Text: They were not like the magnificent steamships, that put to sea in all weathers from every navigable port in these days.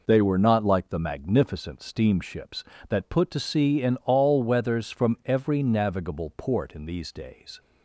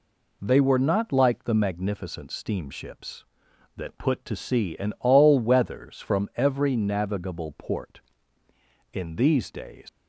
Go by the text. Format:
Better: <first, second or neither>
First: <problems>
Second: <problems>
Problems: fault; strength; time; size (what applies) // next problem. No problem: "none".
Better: first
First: none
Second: leaves "days" unfinished; at 9.8 s; 100 ms